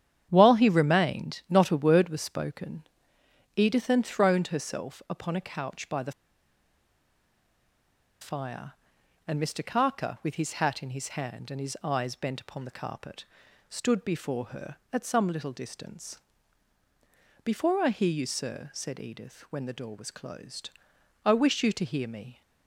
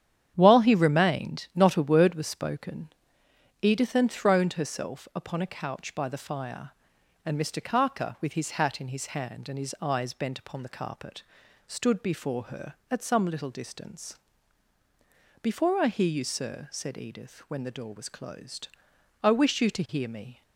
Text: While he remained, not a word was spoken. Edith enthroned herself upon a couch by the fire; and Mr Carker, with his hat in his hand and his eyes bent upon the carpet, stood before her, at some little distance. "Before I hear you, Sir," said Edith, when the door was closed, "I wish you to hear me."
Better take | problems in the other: second | starts louder than the rest; strong; until 1.3 s; 9.5 dB; strong in the second // pauses between "the" and "fire"; strong; at 6.1 s; 2.0 s long

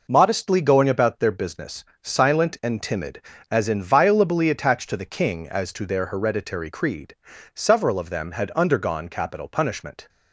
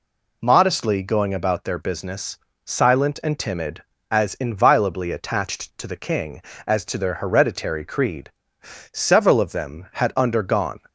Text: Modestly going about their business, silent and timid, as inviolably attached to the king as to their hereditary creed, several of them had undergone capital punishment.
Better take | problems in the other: first | stops before "capital punishment"; at 10.8 s

